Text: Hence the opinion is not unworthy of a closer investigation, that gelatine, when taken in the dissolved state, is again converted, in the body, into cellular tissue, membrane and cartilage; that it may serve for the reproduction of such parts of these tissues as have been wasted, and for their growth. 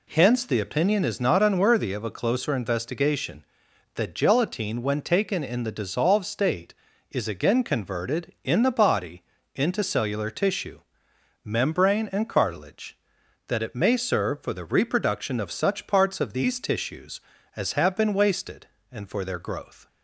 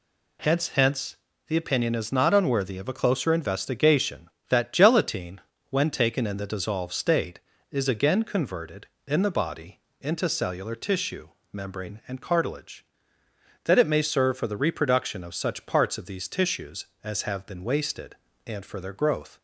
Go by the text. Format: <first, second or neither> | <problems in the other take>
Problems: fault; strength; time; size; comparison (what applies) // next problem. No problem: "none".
first | says "Hence" twice; at 0.6 s